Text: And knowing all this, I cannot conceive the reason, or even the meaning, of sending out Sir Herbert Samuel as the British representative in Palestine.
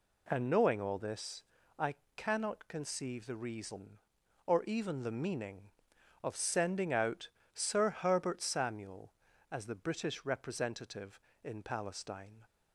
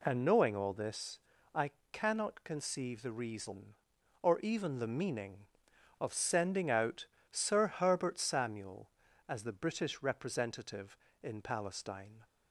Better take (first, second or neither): neither